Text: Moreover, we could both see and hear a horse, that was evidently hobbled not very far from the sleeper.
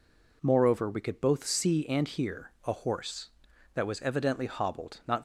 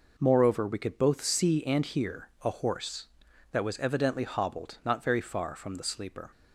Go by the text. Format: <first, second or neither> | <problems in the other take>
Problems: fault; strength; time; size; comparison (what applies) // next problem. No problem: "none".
second | stops before "very far from the sleeper"; at 5.1 s